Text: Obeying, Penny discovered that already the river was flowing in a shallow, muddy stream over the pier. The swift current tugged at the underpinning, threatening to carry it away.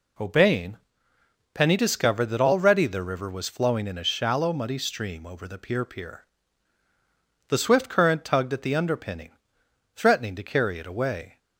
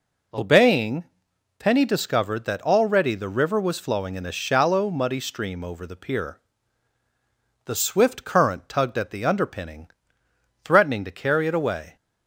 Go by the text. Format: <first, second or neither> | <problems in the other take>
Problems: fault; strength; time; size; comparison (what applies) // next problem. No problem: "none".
second | says "pier" twice; at 5.8 s